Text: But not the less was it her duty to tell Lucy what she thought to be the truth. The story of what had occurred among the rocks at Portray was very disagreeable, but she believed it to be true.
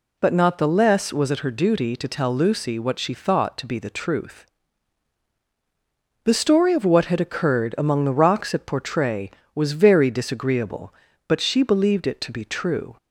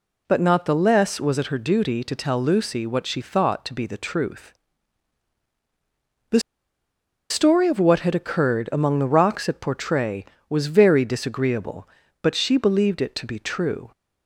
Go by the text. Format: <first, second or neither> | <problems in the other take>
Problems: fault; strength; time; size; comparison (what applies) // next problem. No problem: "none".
first | pauses between "The" and "story"; noticeable; at 6.3 s; 0.91 s long